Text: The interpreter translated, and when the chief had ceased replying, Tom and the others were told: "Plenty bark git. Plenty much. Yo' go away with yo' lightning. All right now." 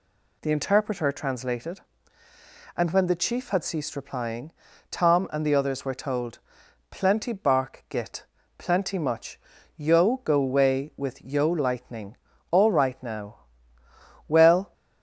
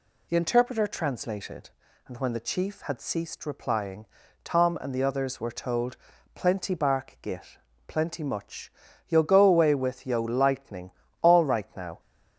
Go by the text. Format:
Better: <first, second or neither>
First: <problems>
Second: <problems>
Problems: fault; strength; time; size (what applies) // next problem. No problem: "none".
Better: second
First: goes on to say "Well"; slight; from 14.2 s on; 0.46 s long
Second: none